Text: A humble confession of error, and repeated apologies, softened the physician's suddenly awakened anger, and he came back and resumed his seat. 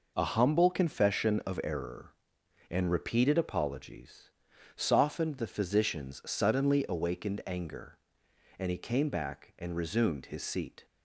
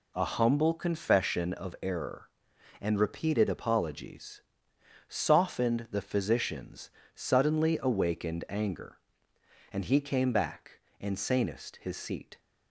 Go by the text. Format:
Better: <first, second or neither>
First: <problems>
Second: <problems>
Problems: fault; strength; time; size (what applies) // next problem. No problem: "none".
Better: first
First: none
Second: pauses between "physician's" and "suddenly"; slight; at 6.9 s; 0.24 s long // says "sanest" for "resumed"; at 11.1 s